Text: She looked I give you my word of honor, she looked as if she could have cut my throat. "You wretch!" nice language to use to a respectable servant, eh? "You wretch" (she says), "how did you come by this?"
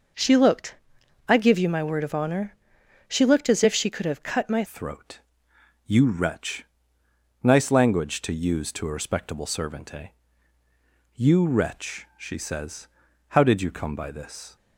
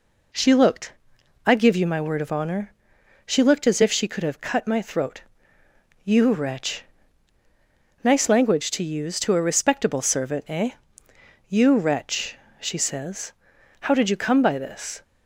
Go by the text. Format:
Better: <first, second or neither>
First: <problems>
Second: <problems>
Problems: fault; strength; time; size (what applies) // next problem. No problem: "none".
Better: second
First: pauses between "looked" and "I"; noticeable; at 0.7 s; 0.52 s long // changes voice at "throat"; from 4.6 s on; 9.9 s long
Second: pauses between "looked" and "I"; noticeable; at 0.9 s; 0.52 s long